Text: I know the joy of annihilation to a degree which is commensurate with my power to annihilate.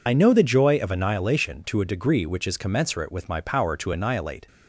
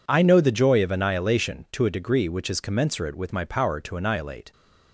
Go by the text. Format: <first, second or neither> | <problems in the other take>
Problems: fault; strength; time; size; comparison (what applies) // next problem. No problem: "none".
second | loses the start of "I"; at 0.0 s; 40 ms